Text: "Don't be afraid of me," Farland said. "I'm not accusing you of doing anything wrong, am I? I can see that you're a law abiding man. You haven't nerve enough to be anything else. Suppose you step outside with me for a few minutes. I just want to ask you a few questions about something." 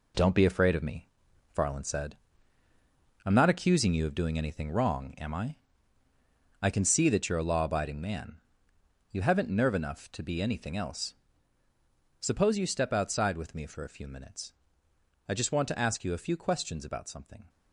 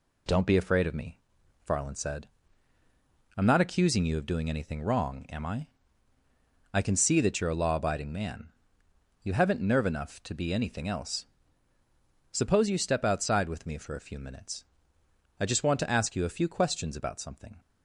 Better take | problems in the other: second | gets quieter; strong; throughout; 7.5 dB

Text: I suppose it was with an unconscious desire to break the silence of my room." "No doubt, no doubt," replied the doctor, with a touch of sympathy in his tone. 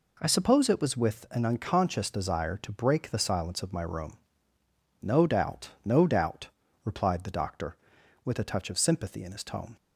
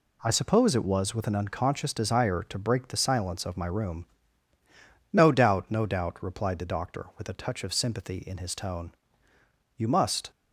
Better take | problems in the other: first | goes on to say "You must"; from 9.7 s on; 0.52 s long

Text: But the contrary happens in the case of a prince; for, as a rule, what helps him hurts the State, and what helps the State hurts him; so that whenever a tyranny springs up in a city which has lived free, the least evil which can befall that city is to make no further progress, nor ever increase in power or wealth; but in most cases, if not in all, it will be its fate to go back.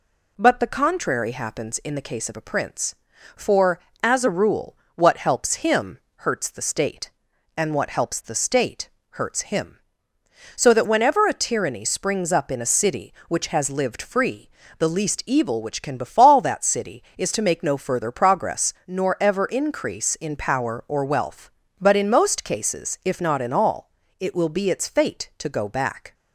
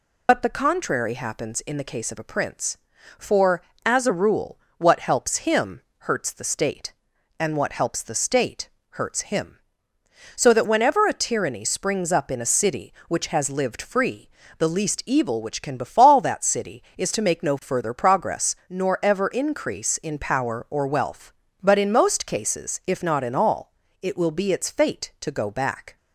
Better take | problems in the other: first | loses the start of "But"; at 0.2 s; 95 ms // pauses between "him" and "hurts"; slight; at 5.8 s; 0.18 s long; slight in the first // pauses between "State" and "hurts"; slight; at 8.6 s; 0.22 s long; slight in the first

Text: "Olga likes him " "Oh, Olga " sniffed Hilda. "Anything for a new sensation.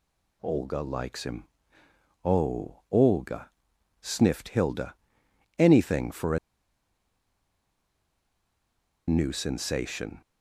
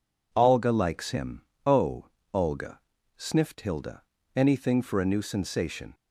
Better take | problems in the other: second | pauses between "a" and "new"; strong; at 6.3 s; 2.7 s long

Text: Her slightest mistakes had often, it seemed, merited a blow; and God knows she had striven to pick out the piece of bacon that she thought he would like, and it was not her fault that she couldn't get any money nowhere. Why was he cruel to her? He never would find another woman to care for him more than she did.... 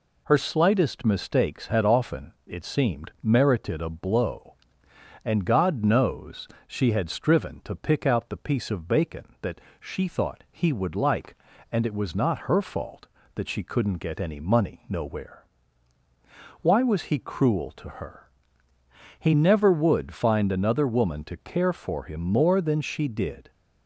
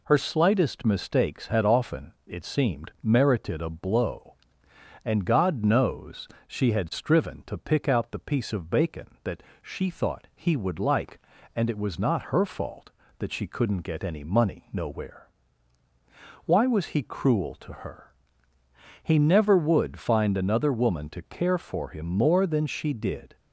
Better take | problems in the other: neither | pauses between "knows" and "she"; slight; the same in both // pauses between "that" and "she"; slight; the same in both

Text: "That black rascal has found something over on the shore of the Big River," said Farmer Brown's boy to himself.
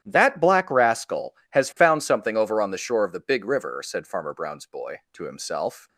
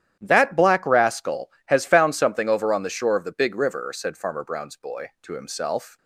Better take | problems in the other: neither | starts louder than the rest; strong; the same in both

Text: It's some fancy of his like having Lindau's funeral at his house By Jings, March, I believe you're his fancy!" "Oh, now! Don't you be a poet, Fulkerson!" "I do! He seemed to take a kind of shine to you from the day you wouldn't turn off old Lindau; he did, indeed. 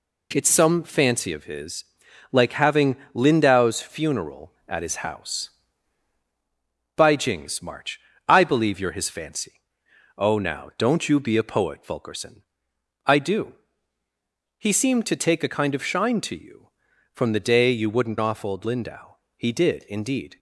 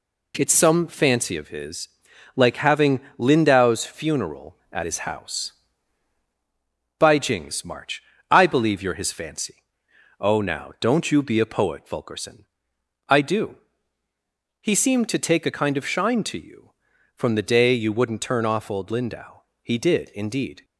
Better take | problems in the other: second | pauses between "his" and "like"; noticeable; at 1.8 s; 0.50 s long; noticeable in the second // pauses between "having" and "Lindau's"; slight; at 2.9 s; 0.18 s long; slight in the second // skips "turn"; at 18.1 s

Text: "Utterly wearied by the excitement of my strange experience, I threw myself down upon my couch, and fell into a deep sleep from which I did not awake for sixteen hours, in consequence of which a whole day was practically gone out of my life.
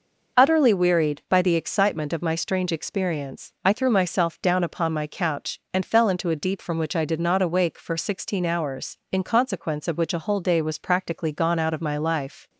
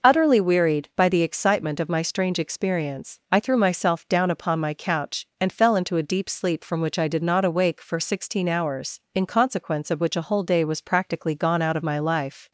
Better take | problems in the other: second | skips "sleep"; at 6.6 s

